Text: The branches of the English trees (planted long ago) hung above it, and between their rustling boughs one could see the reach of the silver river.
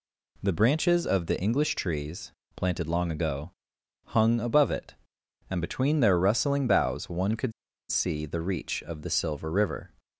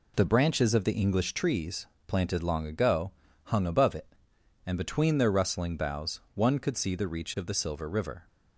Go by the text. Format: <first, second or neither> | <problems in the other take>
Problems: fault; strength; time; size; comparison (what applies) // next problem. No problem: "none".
second | pauses between "could" and "see"; at 7.5 s; 0.39 s long